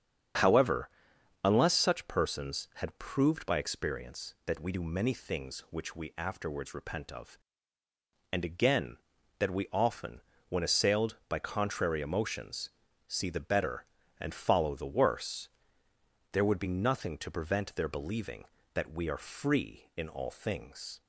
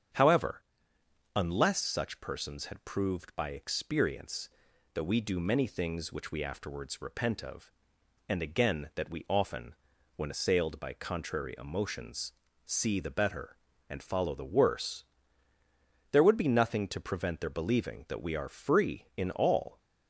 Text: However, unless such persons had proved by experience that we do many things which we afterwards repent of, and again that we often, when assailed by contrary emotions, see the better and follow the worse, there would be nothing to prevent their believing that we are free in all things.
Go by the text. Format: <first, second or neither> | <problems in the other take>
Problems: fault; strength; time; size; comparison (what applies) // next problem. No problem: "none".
first | starts louder than the rest; strong; until 1.8 s; 8 dB; strong in the first // stops before "things"; at 19.7 s